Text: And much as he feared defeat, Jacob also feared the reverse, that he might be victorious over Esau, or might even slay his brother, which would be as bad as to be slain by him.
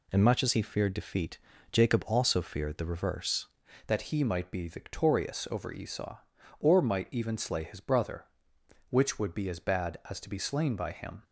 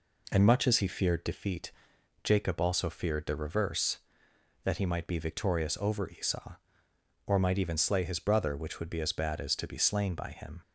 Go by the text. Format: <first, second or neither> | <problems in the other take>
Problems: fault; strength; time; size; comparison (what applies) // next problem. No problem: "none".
second | changes voice at "that"; from 3.8 s on; 7.4 s long